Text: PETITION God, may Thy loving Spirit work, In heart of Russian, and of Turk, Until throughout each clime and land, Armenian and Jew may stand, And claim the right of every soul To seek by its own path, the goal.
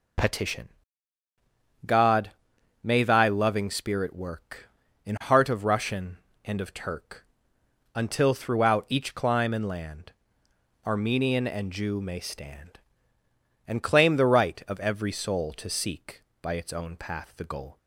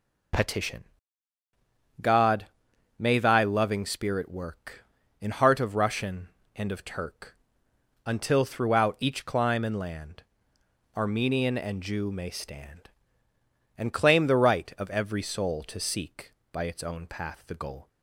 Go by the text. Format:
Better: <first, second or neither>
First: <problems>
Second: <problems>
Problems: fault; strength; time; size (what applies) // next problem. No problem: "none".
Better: neither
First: pauses between "PETITION" and "God"; at 0.6 s; 1.1 s long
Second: pauses between "PETITION" and "God"; at 0.8 s; 1.1 s long